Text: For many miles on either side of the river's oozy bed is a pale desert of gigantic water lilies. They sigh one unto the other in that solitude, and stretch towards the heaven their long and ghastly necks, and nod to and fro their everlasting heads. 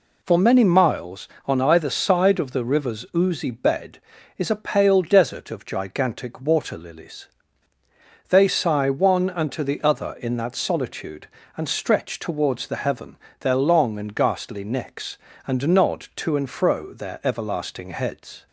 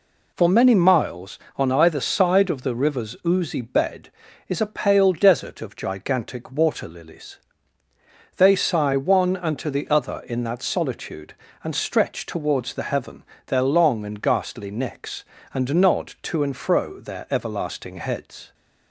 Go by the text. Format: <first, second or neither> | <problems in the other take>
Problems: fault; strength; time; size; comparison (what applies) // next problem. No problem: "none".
neither | pauses between "heaven" and "their"; slight; the same in both